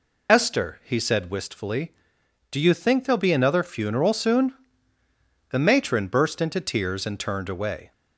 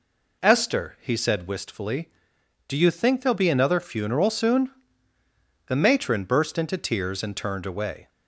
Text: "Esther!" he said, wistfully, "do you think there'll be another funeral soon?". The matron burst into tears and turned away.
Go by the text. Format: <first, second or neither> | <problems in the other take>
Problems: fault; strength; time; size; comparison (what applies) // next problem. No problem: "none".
second | loses the start of "Esther"; at 0.2 s; 65 ms